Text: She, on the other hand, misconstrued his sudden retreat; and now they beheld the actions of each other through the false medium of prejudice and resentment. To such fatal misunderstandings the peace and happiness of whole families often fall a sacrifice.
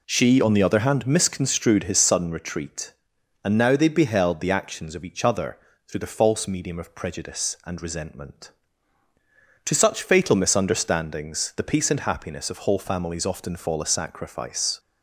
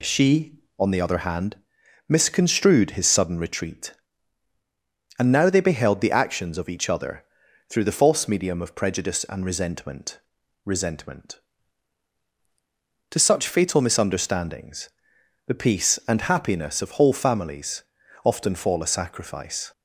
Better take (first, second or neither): first